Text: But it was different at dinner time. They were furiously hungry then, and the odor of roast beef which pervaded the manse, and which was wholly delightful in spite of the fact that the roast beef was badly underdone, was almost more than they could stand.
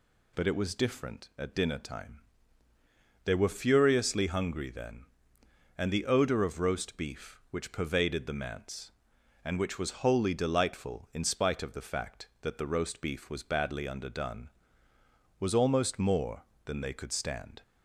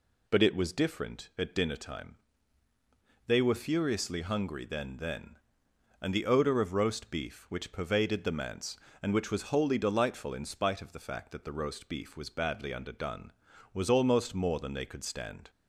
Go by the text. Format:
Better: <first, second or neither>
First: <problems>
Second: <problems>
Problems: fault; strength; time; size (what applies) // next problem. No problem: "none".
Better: first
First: none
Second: says "then" twice; at 4.9 s